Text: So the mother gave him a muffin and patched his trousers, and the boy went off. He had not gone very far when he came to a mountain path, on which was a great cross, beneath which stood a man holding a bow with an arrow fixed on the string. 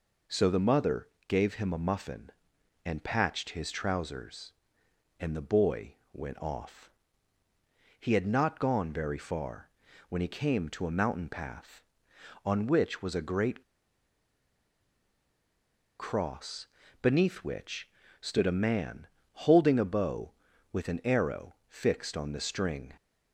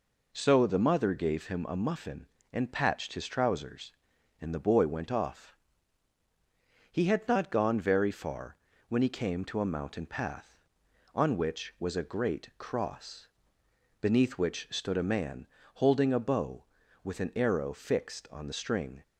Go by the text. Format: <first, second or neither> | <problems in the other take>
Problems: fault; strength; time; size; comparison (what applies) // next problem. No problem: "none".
second | pauses between "mother" and "gave"; slight; at 1.0 s; 0.20 s long // pauses between "boy" and "went"; slight; at 5.9 s; 0.16 s long // pauses between "far" and "when"; at 9.6 s; 0.40 s long; slight in the second // pauses between "great" and "cross"; strong; at 13.6 s; 2.3 s long // pauses between "which" and "stood"; slight; at 17.8 s; 0.32 s long // pauses between "man" and "holding"; slight; at 19.0 s; 0.24 s long; slight in the second